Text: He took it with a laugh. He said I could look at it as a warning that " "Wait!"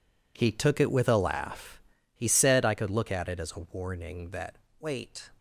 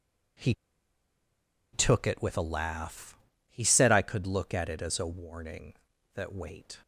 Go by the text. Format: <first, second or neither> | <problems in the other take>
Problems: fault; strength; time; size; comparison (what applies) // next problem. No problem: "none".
first | pauses between "He" and "took"; at 0.5 s; 1.1 s long